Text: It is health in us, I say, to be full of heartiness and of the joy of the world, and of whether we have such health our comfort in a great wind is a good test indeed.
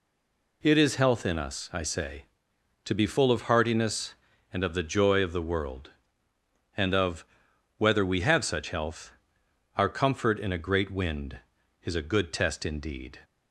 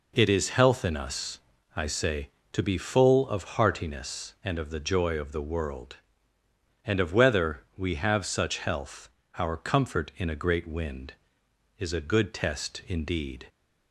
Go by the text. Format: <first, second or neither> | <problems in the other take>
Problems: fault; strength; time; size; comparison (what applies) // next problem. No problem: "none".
second | stays silent before the first word; slight; until 0.6 s; 0.6 s long // pauses between "of" and "whether"; noticeable; at 7.2 s; 0.52 s long // pauses between "health" and "our"; noticeable; at 9.1 s; 0.64 s long; slight in the second